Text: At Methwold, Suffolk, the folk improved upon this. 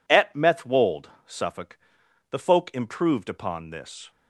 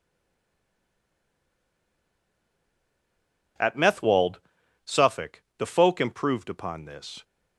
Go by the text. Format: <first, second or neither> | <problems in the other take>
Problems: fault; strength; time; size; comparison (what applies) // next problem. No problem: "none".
first | stays silent before the first word; strong; until 3.5 s; 3.5 s long